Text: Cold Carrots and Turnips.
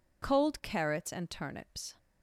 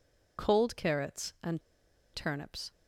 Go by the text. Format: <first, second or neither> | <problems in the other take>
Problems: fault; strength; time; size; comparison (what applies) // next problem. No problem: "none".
first | pauses between "and" and "Turnips"; noticeable; at 1.6 s; 0.52 s long